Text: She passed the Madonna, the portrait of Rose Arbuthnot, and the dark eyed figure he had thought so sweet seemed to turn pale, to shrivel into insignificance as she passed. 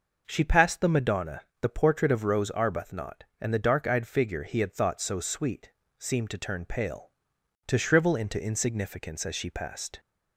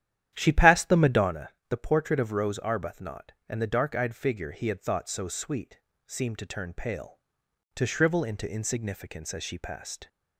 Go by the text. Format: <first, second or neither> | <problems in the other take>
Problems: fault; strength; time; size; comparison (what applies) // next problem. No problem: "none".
first | starts louder than the rest; strong; until 1.4 s; 11 dB // pauses between "sweet" and "seemed"; slight; at 5.7 s; 0.26 s long; slight in the first